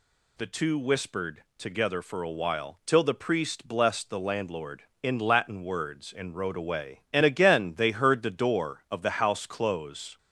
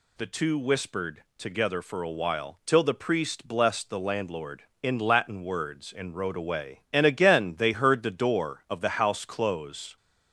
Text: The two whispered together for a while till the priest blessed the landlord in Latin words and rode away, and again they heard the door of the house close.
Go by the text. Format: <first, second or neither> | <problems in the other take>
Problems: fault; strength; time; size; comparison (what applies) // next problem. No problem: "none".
neither | none